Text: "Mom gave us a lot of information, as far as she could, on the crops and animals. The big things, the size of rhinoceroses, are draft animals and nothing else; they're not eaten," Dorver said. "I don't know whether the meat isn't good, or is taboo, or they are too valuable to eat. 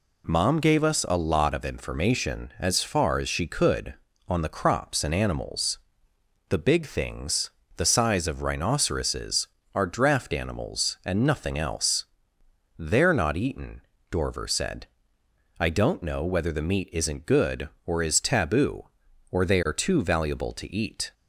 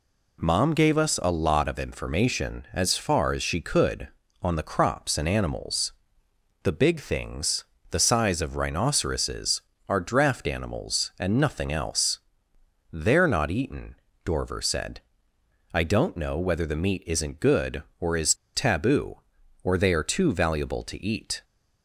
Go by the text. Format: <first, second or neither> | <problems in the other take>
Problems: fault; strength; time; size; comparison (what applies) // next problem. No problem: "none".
first | pauses between "is" and "taboo"; slight; at 18.3 s; 0.21 s long